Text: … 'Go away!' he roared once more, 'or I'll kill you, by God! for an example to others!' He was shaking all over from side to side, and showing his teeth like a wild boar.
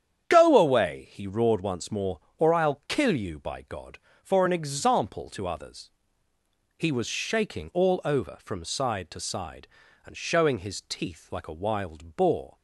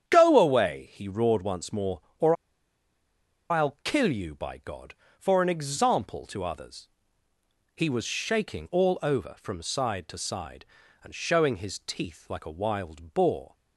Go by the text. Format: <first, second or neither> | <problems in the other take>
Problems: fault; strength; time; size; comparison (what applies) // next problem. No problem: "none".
first | starts louder than the rest; strong; until 1.1 s; 9 dB; strong in the first // pauses between "or" and "I'll"; at 2.3 s; 1.1 s long